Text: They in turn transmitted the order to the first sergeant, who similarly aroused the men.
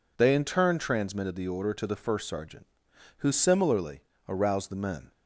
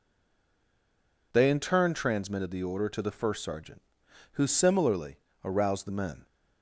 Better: first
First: pauses between "similarly" and "aroused"; slight; at 4.0 s; 0.26 s long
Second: stays silent before the first word; noticeable; until 1.3 s; 1.3 s long // pauses between "similarly" and "aroused"; slight; at 5.1 s; 0.26 s long

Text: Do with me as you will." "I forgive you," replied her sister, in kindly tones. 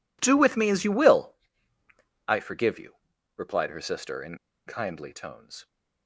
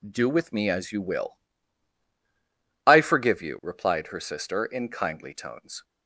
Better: second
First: pauses between "in" and "kindly"; slight; at 4.3 s; 0.30 s long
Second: none

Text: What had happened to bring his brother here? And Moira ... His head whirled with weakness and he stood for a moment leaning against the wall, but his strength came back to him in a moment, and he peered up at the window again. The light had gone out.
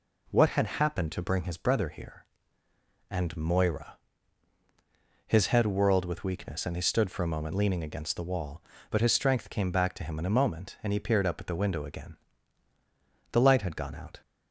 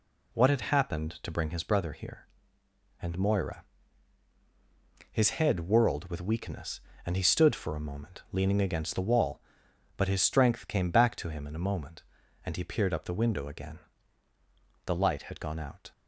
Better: first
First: none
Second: skips "at"; at 13.0 s

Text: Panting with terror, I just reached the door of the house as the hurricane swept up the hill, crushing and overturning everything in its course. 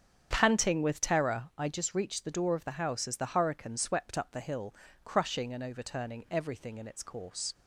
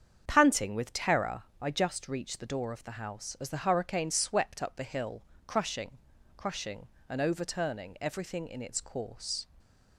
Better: first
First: starts louder than the rest; strong; until 1.3 s; 8 dB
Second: starts louder than the rest; strong; until 1.2 s; 7.5 dB // says "crushing" twice; at 6.3 s

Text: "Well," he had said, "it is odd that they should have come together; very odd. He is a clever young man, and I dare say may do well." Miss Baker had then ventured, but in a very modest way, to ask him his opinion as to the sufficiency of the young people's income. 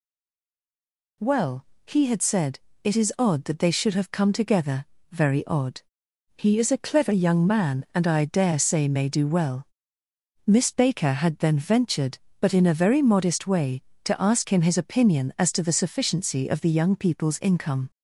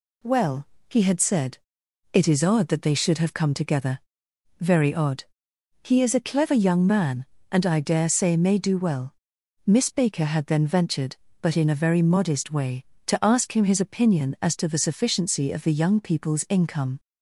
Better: second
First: stays silent before the first word; noticeable; until 1.2 s; 1.2 s long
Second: none

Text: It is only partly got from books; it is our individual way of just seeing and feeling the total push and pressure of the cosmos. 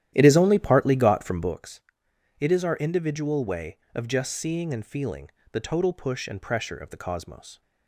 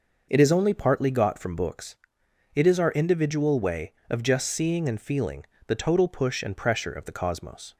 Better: second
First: starts louder than the rest; strong; until 1.5 s; 12 dB // pauses between "feeling" and "the"; slight; at 5.3 s; 0.22 s long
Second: pauses between "feeling" and "the"; slight; at 5.4 s; 0.22 s long

